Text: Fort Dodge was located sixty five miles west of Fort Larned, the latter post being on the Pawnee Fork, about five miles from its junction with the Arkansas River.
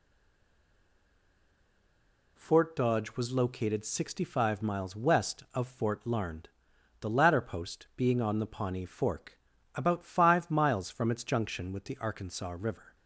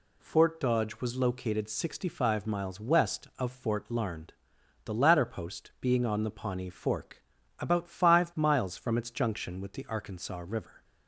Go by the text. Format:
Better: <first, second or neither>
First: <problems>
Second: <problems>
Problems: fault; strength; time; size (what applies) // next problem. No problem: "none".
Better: second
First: stays silent before the first word; until 2.3 s; 2.3 s long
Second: none